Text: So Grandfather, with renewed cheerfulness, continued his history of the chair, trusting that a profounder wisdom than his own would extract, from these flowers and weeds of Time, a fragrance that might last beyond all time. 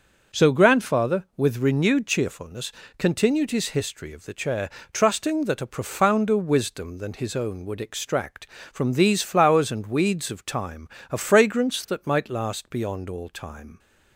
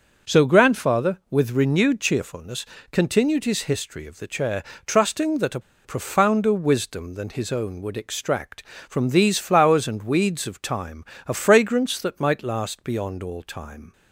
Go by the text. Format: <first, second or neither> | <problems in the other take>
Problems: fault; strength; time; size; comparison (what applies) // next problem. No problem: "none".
first | starts louder than the rest; noticeable; until 1.3 s; 6 dB; also in the first // pauses between "a" and "profounder"; slight; at 5.5 s; 0.25 s long